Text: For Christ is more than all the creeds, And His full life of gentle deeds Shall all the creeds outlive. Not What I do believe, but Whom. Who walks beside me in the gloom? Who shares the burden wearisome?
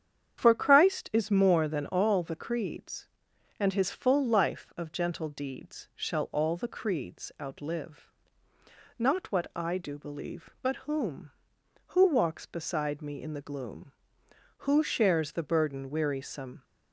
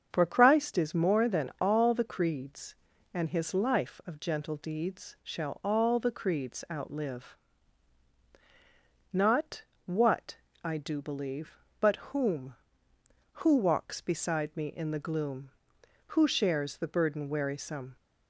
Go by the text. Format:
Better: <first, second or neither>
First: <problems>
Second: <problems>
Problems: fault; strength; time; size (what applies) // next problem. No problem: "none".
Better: first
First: starts louder than the rest; strong; until 1.4 s; 8.5 dB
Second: starts louder than the rest; strong; until 1.1 s; 7 dB // skips "full"; at 3.5 s // pauses between "Not" and "What"; slight; at 9.6 s; 0.24 s long // pauses between "What" and "I"; slight; at 10.3 s; 0.28 s long